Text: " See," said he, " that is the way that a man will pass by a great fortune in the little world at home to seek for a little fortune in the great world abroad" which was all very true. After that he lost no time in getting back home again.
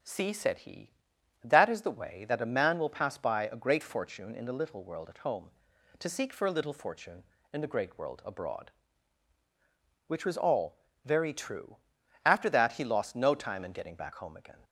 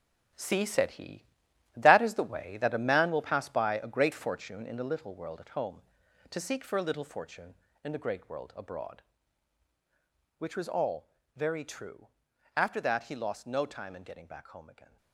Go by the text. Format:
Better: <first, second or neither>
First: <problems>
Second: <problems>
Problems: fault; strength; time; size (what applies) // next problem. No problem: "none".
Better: first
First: pauses between "all" and "very"; slight; at 10.7 s; 0.30 s long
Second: gets quieter; throughout; 7 dB // pauses between "all" and "very"; slight; at 11.0 s; 0.30 s long